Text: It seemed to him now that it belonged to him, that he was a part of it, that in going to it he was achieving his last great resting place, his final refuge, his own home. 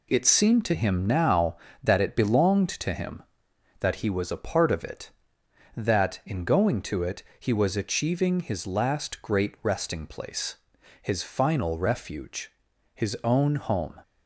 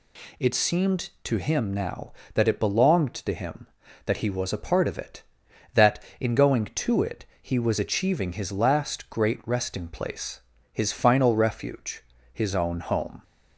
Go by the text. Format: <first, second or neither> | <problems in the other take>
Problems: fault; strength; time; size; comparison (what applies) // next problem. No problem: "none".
neither | pauses between "it" and "he"; slight; the same in both